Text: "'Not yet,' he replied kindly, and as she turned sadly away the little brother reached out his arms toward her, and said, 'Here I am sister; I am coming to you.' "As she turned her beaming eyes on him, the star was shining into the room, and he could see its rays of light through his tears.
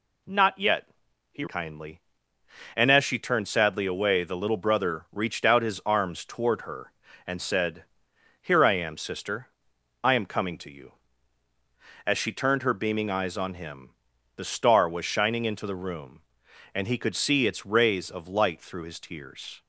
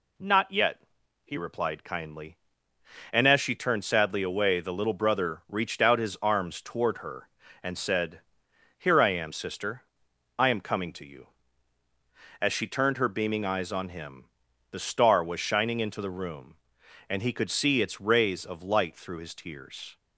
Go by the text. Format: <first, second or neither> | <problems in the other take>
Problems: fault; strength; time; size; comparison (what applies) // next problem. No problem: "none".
second | skips "replied"; at 1.4 s